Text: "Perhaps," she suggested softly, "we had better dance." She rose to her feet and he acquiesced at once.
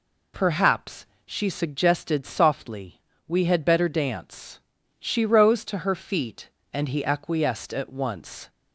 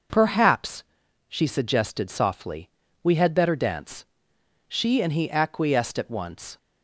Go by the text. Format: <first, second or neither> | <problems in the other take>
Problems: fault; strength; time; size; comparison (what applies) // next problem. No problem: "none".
first | skips "rose to her feet"; at 5.0 s